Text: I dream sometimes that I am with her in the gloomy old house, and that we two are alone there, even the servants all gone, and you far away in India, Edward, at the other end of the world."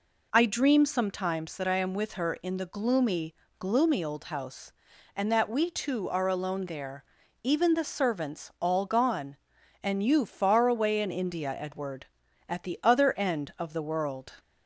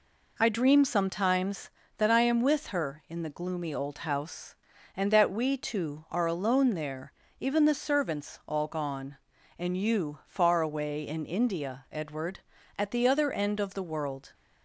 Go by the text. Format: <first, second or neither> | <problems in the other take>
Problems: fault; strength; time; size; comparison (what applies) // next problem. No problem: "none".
second | says "gloomy" twice; at 3.5 s